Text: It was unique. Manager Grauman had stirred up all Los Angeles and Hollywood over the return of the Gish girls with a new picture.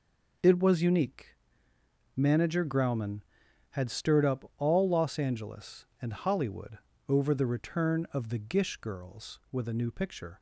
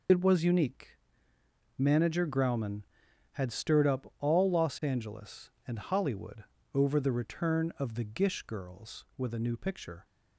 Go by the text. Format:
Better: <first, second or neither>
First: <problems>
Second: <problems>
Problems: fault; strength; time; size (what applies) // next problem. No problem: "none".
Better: first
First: pauses between "Hollywood" and "over"; slight; at 6.7 s; 0.30 s long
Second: loses the start of "It"; at 0.0 s; 75 ms // pauses between "Hollywood" and "over"; slight; at 6.4 s; 0.30 s long